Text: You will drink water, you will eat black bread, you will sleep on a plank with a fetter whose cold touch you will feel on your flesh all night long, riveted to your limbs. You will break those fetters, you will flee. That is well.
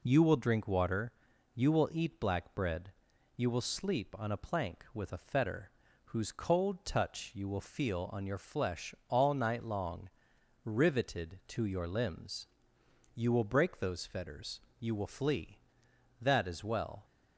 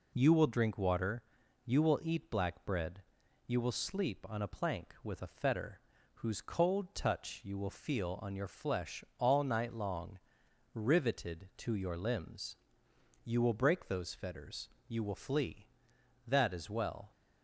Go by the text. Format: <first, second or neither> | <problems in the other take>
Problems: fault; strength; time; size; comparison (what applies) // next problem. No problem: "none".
neither | pauses between "fetter" and "whose"; slight; the same in both